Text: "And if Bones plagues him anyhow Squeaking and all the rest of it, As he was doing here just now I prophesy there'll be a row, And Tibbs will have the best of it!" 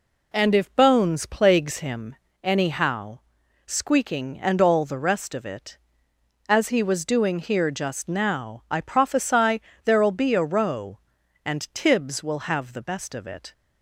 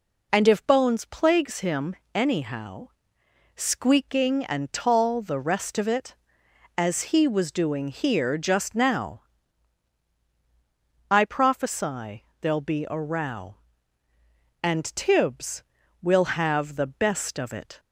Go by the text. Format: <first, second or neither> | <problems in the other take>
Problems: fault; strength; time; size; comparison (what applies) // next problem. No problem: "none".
first | pauses between "him" and "anyhow"; slight; at 1.9 s; 0.18 s long; slight in the first // pauses between "anyhow" and "Squeaking"; noticeable; at 2.8 s; 0.68 s long; noticeable in the first // says "tall" for "all"; at 4.7 s // pauses between "now" and "I"; strong; at 9.2 s; 1.8 s long // pauses between "prophesy" and "there'll"; slight; at 12.2 s; 0.16 s long; slight in the first